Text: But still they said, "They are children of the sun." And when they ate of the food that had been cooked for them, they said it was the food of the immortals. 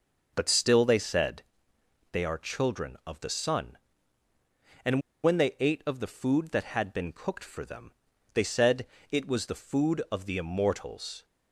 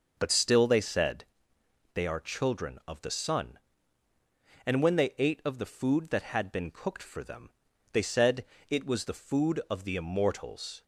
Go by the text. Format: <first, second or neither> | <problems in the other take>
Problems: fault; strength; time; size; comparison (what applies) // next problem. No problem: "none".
second | pauses between "And" and "when"; slight; at 5.0 s; 0.23 s long // pauses between "said" and "it"; slight; at 8.8 s; 0.24 s long; slight in the second